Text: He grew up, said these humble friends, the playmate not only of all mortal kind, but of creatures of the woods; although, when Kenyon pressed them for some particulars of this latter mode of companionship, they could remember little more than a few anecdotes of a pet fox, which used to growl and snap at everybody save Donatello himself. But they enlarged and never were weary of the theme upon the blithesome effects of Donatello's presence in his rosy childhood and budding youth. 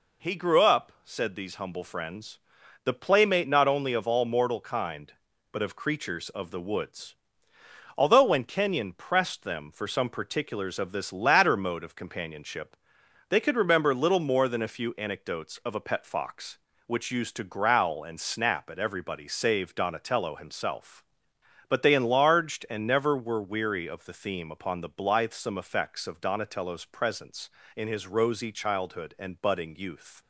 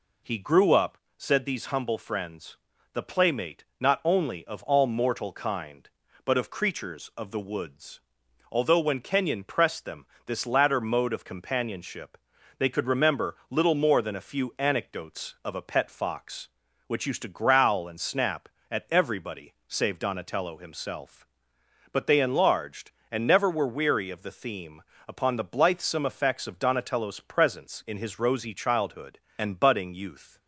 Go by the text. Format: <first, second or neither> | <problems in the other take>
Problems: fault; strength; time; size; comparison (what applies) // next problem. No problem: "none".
first | skips "for some particulars of"; at 10.1 s // pauses between "everybody" and "save"; slight; at 19.5 s; 0.16 s long // pauses between "theme" and "upon"; slight; at 24.8 s; 0.26 s long